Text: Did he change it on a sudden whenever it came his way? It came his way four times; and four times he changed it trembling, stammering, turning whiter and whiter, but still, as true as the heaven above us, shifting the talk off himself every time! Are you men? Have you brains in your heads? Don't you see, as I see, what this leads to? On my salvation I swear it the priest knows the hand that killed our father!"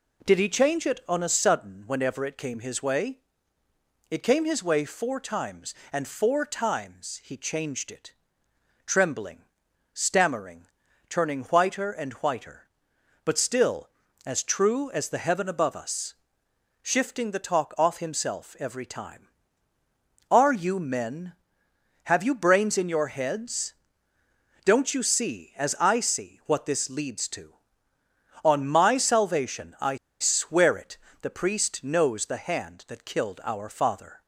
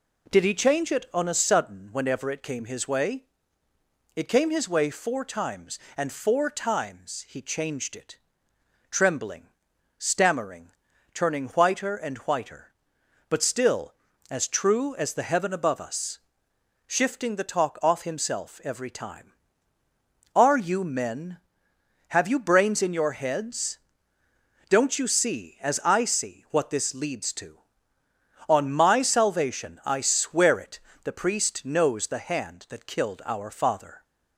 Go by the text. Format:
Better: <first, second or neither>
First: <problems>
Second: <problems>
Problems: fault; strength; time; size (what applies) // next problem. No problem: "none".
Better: second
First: pauses between "it" and "trembling"; noticeable; at 8.1 s; 0.74 s long // pauses between "I" and "swear"; slight; at 29.9 s; 0.25 s long // pauses between "it" and "the"; slight; at 30.9 s; 0.24 s long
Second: pauses between "it" and "trembling"; noticeable; at 8.1 s; 0.74 s long // pauses between "it" and "the"; slight; at 30.7 s; 0.24 s long